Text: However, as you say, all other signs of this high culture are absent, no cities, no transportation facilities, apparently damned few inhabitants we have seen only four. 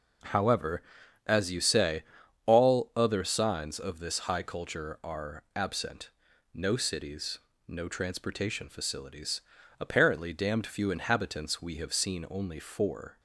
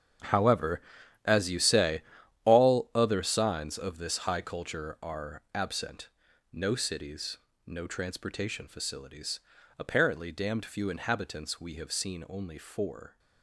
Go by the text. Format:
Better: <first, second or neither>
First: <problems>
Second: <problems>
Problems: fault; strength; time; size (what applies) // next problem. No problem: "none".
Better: first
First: none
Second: gets quieter; strong; throughout; 14 dB